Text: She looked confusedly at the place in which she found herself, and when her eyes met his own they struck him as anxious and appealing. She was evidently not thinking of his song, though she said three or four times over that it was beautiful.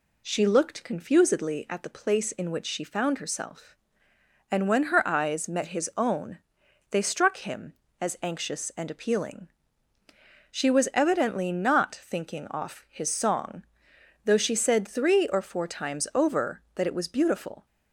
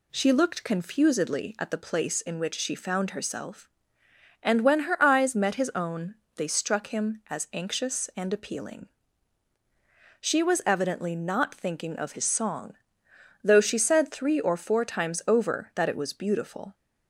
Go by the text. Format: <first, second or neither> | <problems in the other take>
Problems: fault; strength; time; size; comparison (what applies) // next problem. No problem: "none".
second | pauses between "own" and "they"; noticeable; at 6.3 s; 0.54 s long; slight in the second // says "off" for "of"; at 12.5 s